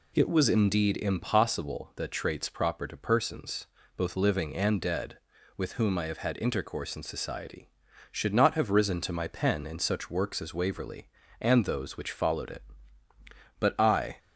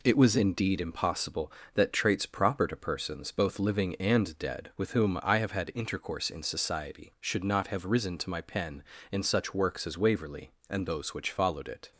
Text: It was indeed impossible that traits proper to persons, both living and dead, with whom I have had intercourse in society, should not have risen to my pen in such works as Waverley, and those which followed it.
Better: second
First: goes on to say "But I"; from 13.5 s on; 0.60 s long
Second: none

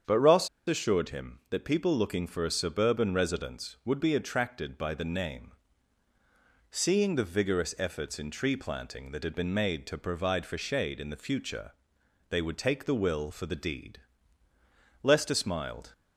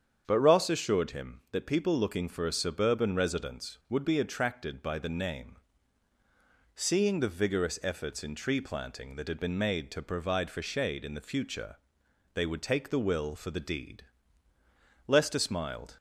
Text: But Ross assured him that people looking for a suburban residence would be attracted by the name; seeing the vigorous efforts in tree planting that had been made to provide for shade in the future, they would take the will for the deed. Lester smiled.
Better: second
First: starts louder than the rest; strong; until 1.2 s; 7.5 dB // pauses between "Ross" and "assured"; slight; at 0.4 s; 0.19 s long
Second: starts louder than the rest; strong; until 1.2 s; 8 dB

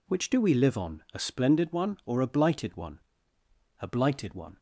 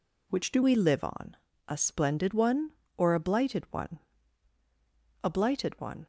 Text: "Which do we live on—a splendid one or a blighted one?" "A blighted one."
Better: first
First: none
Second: changes voice at "we"; from 0.6 s on; 5.4 s long

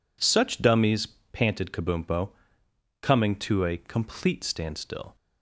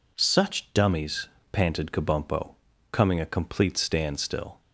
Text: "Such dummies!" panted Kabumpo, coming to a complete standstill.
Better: first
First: none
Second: skips "to"; at 3.1 s

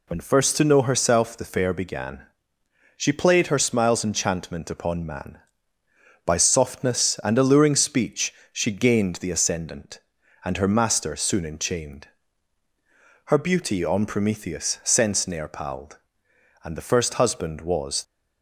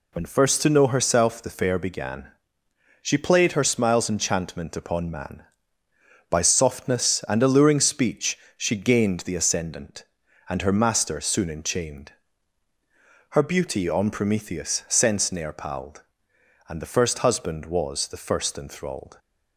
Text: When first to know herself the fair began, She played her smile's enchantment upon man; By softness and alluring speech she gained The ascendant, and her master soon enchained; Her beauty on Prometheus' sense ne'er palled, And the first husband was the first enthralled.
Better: second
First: pauses between "speech" and "she"; slight; at 8.3 s; 0.22 s long // stops before "the first enthralled"; at 18.0 s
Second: pauses between "speech" and "she"; slight; at 8.3 s; 0.22 s long

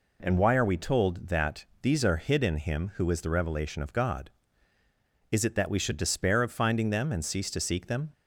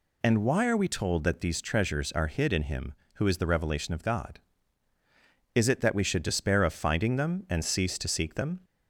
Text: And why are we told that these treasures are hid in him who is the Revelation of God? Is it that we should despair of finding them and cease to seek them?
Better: second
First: pauses between "that" and "these"; slight; at 1.6 s; 0.16 s long // skips "treasures"; at 2.0 s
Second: none

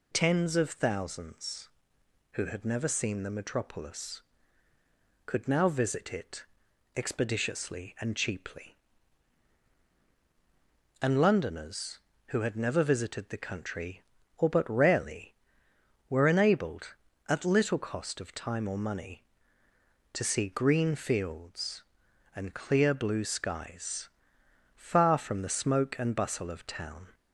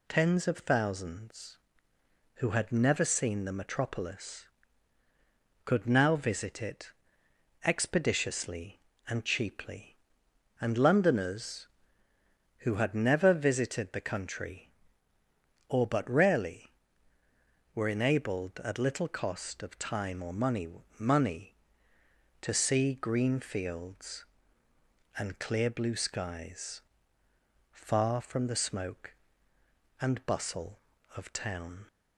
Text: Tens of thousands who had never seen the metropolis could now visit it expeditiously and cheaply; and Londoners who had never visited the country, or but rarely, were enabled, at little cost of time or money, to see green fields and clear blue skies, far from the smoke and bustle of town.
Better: first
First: pauses between "it" and "expeditiously"; noticeable; at 6.4 s; 0.54 s long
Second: pauses between "it" and "expeditiously"; noticeable; at 6.9 s; 0.74 s long // says "money" twice; at 20.9 s

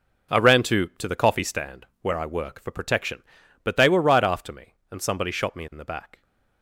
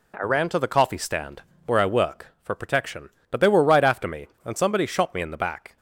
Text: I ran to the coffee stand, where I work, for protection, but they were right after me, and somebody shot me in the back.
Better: second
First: says "to" twice; at 0.9 s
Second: none

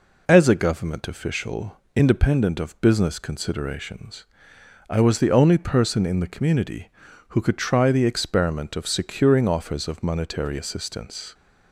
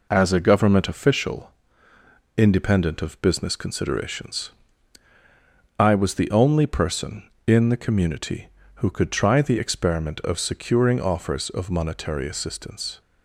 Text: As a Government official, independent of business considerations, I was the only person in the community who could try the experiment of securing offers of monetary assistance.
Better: neither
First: none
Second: none

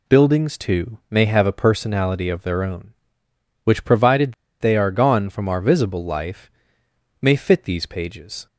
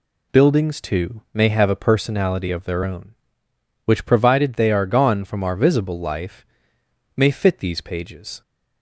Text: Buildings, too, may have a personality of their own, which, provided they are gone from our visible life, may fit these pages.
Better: second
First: pauses between "provided" and "they"; slight; at 4.3 s; 0.26 s long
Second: none

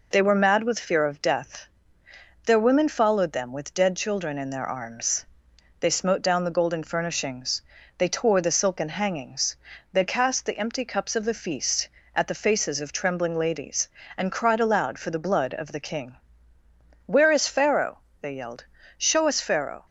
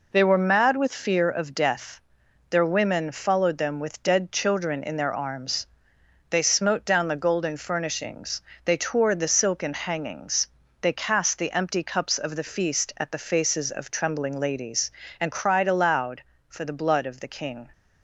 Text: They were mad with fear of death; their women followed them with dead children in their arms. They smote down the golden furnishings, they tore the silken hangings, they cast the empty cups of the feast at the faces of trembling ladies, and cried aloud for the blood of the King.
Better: second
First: goes on to say "Where is Pharaoh they yelled show us Pharaoh"; strong; from 17.0 s on; 2.8 s long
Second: none

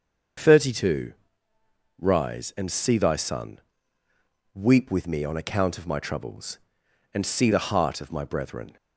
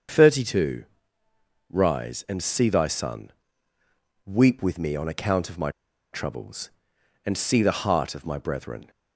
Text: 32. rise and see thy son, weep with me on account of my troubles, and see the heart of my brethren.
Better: first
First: starts louder than the rest; until 2.2 s; 6.5 dB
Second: starts louder than the rest; until 1.9 s; 6.5 dB // pauses between "my" and "troubles"; at 5.6 s; 0.43 s long

